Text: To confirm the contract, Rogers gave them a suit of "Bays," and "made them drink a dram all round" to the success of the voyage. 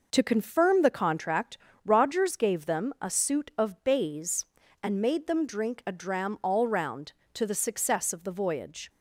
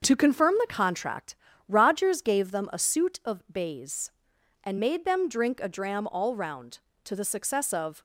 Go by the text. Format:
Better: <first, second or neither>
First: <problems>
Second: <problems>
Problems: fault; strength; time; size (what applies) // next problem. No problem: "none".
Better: first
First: none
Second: starts louder than the rest; until 1.0 s; 6.5 dB // stops before "the voyage"; at 7.9 s